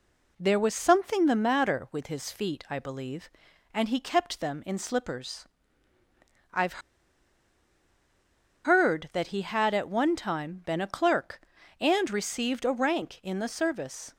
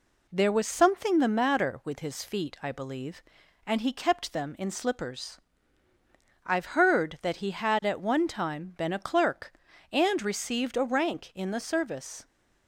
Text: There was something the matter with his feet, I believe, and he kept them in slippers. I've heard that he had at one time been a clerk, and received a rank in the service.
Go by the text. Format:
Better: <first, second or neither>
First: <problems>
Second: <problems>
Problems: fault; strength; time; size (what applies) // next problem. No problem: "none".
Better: second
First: pauses between "I've" and "heard"; strong; at 6.8 s; 1.8 s long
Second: none